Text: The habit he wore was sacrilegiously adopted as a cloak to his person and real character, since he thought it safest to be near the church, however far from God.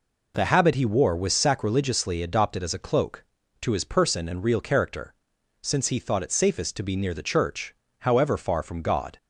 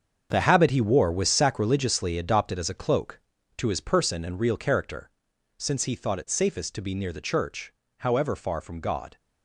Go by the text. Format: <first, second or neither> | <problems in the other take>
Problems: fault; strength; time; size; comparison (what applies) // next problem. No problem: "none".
first | gets quieter; strong; throughout; 11 dB